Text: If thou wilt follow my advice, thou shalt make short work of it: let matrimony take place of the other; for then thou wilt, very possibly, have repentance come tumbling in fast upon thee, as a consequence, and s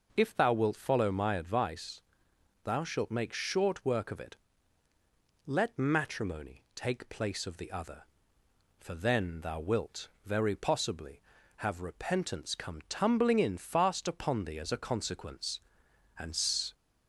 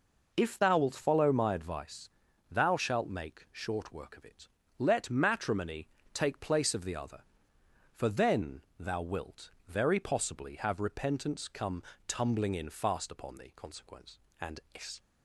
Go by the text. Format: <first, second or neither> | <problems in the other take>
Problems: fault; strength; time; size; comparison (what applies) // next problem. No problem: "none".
first | pauses between "matrimony" and "take"; slight; at 5.8 s; 0.26 s long // pauses between "then" and "thou"; slight; at 8.6 s; 0.16 s long // pauses between "come" and "tumbling"; slight; at 11.8 s; 0.26 s long // skips "as a"; at 13.5 s // pauses between "and" and "s"; slight; at 14.5 s; 0.16 s long